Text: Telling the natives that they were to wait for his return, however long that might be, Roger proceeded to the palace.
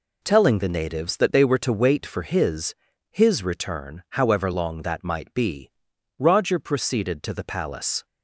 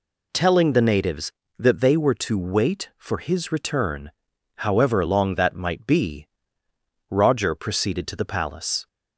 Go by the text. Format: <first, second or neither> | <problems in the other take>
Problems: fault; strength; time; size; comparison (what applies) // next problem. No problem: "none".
second | says "his" twice; at 3.1 s